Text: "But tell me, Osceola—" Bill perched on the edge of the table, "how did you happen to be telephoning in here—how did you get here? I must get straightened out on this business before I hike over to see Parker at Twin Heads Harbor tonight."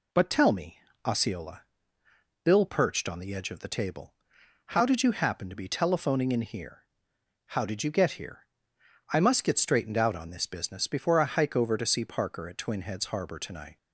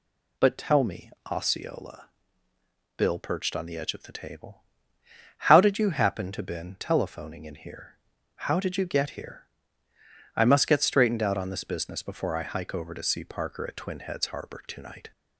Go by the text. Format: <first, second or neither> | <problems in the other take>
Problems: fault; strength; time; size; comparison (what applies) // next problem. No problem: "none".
first | says "been" for "be"; at 6.4 s